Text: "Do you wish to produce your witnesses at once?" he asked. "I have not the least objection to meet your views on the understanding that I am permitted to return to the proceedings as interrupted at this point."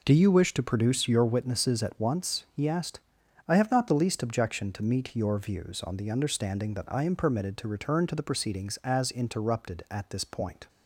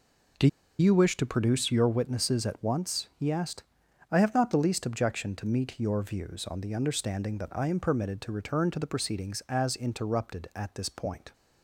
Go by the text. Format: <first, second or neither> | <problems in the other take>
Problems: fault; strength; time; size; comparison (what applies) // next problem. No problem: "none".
first | pauses between "Do" and "you"; slight; at 0.4 s; 0.31 s long